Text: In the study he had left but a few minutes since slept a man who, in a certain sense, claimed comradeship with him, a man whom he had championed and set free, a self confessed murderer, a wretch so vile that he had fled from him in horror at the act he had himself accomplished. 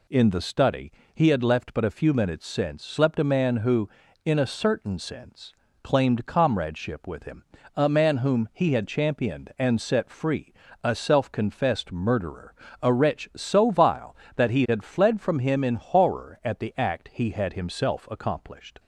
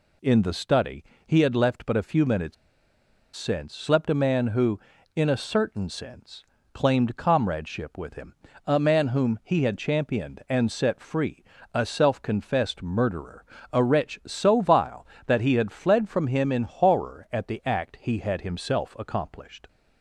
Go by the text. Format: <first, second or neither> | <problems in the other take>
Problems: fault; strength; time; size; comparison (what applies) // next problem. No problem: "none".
first | pauses between "study" and "he"; slight; at 1.0 s; 0.24 s long; slight in the first // pauses between "minutes" and "since"; noticeable; at 2.5 s; 0.80 s long